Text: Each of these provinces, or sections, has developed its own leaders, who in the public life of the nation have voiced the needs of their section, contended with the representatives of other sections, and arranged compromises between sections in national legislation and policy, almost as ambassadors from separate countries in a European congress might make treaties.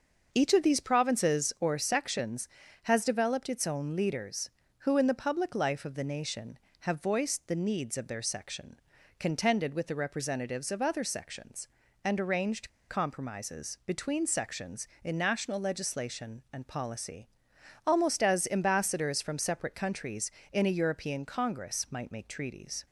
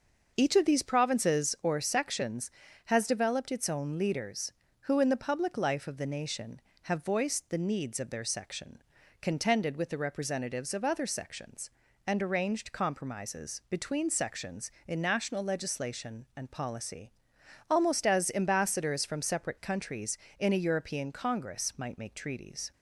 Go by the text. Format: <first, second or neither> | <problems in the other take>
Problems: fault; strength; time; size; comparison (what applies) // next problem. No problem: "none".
second | starts louder than the rest; until 1.3 s; 6 dB; also in the second // pauses between "arranged" and "compromises"; slight; at 12.7 s; 0.19 s long